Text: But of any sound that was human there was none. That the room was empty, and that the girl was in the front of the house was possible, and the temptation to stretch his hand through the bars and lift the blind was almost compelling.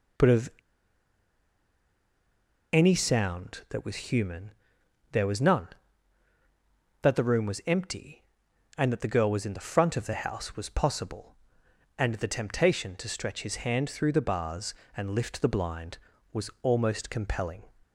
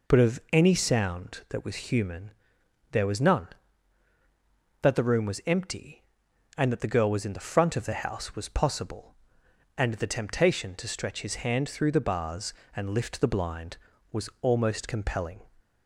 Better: second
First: pauses between "of" and "any"; strong; at 0.4 s; 2.2 s long // pauses between "human" and "there"; noticeable; at 4.5 s; 0.62 s long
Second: pauses between "human" and "there"; noticeable; at 2.3 s; 0.62 s long

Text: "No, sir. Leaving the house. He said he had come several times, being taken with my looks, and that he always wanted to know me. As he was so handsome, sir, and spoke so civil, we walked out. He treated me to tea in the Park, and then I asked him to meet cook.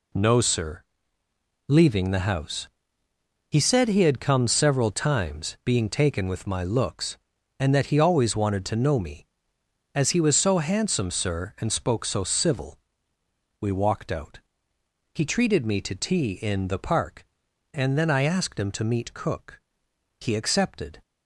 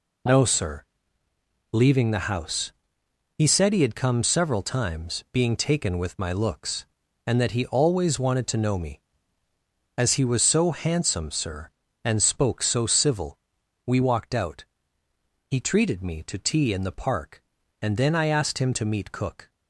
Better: second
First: goes on to say "He accepted"; noticeable; from 20.1 s on; 0.82 s long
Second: none

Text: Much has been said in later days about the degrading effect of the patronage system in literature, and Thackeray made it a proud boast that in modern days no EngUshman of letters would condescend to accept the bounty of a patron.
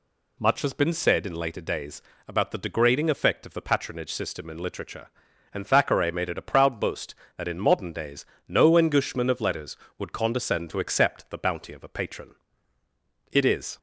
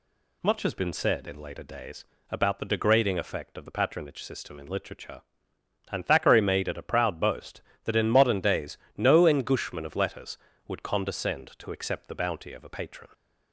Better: second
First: pauses between "days" and "about"; slight; at 2.0 s; 0.26 s long // pauses between "days" and "no"; slight; at 8.2 s; 0.24 s long // goes on to say "It is"; slight; from 13.3 s on; 0.46 s long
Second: pauses between "days" and "about"; slight; at 2.0 s; 0.24 s long // pauses between "days" and "no"; slight; at 8.7 s; 0.18 s long

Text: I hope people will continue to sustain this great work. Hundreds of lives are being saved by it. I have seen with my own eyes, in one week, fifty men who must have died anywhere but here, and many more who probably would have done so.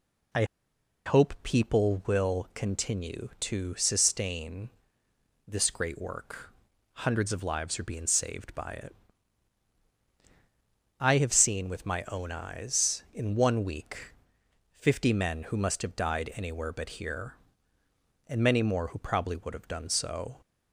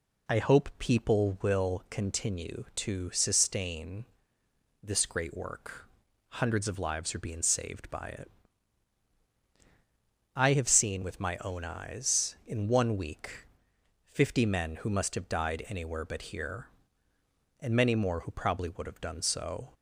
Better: second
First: pauses between "I" and "hope"; noticeable; at 0.4 s; 0.62 s long // pauses between "sustain" and "this"; noticeable; at 4.7 s; 0.76 s long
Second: pauses between "sustain" and "this"; noticeable; at 4.0 s; 0.76 s long

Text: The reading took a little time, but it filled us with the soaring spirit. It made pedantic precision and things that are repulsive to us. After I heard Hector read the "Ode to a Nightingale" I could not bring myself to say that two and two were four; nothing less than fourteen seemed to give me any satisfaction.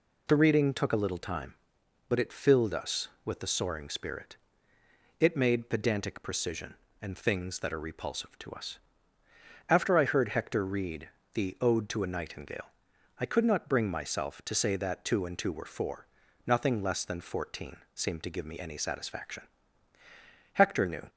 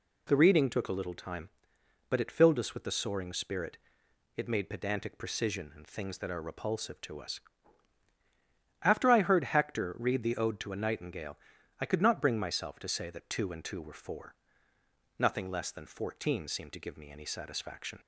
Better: second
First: pauses between "read" and "the"; slight; at 11.0 s; 0.26 s long // pauses between "Nightingale" and "I"; noticeable; at 12.6 s; 0.54 s long // pauses between "fourteen" and "seemed"; slight; at 17.7 s; 0.18 s long // goes on to say "Hector knew"; from 20.5 s on; 0.54 s long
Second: pauses between "Nightingale" and "I"; at 11.3 s; 0.42 s long

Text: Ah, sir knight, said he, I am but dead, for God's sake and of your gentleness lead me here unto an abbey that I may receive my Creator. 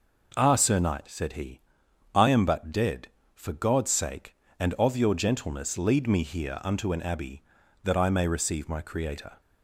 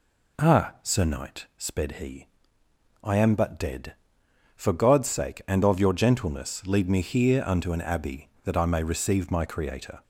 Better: first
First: none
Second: says "sped" for "said"; at 1.5 s

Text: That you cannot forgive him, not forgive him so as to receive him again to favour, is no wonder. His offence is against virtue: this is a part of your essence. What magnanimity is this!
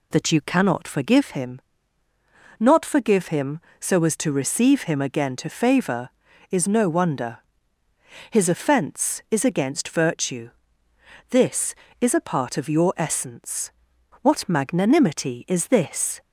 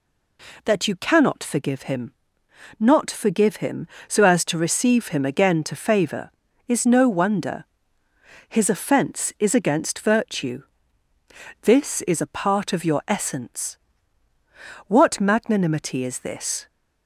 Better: neither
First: none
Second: none

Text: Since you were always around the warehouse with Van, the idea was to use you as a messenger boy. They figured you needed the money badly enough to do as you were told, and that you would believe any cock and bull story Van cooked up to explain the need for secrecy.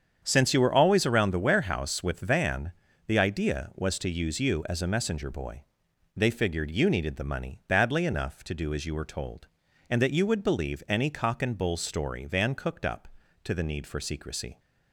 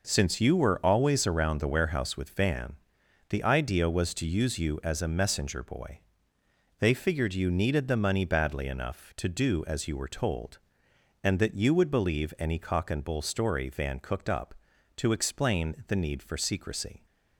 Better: second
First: starts louder than the rest; strong; until 1.2 s; 8 dB // skips "explain"; at 13.5 s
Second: none

